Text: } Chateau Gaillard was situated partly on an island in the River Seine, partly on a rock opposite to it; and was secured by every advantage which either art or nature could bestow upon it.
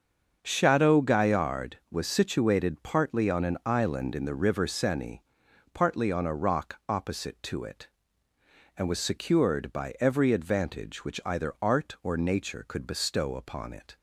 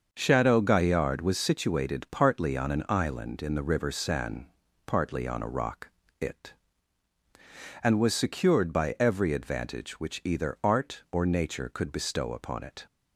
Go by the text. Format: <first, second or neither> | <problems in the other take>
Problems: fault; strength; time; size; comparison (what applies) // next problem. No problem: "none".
first | starts louder than the rest; until 1.1 s; 6.5 dB; also in the first // skips "opposite to"; at 6.0 s